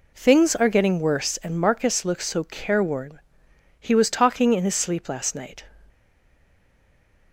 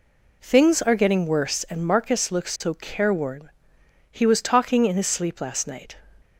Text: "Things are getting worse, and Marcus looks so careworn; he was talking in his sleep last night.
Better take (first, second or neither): second